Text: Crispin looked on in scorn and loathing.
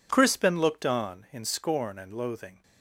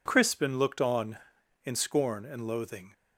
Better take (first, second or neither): neither